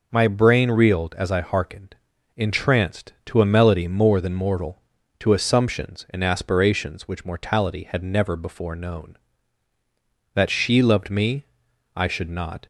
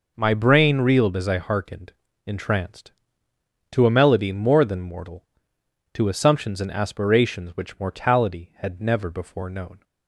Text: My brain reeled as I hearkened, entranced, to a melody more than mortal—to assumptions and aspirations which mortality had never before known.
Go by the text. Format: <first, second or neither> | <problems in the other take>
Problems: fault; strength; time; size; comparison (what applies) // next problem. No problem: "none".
second | goes on to say "That she loved me I should not"; strong; from 10.3 s on; 2.3 s long